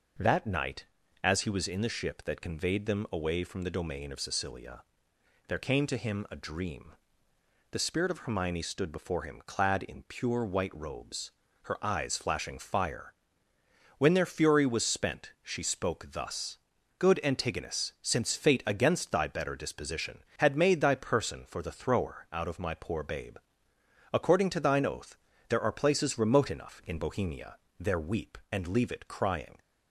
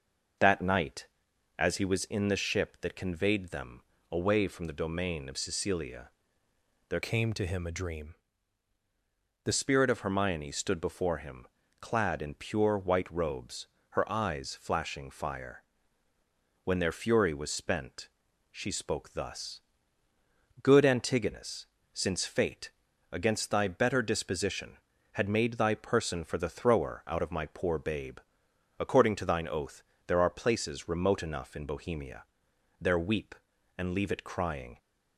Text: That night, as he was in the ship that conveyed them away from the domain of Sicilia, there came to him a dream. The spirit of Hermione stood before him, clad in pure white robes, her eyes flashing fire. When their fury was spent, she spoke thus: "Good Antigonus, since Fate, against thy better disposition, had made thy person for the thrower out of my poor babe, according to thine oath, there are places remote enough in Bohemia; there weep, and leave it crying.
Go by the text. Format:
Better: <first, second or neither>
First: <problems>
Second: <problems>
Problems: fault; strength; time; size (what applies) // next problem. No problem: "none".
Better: first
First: none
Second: pauses between "them" and "away"; slight; at 3.8 s; 0.30 s long // changes voice from "came" to "The"; from 7.0 to 9.5 s; 2.5 s long